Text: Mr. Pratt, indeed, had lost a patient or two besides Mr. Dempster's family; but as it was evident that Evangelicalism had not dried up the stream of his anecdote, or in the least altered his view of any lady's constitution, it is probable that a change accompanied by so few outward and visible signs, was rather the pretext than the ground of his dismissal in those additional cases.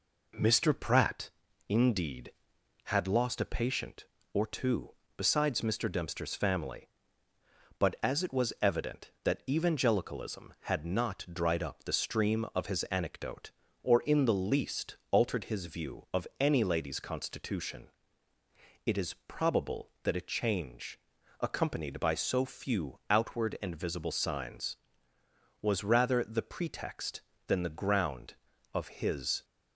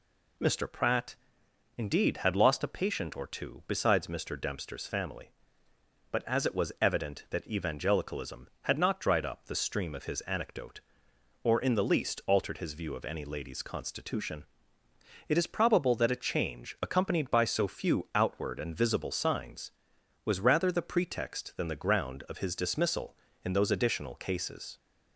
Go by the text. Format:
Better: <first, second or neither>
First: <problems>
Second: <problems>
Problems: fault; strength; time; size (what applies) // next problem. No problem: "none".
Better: second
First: pauses between "two" and "besides"; slight; at 4.9 s; 0.26 s long // pauses between "least" and "altered"; slight; at 14.9 s; 0.16 s long // pauses between "change" and "accompanied"; at 20.9 s; 0.40 s long // stops before "dismissal in those additional cases"; at 29.4 s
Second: none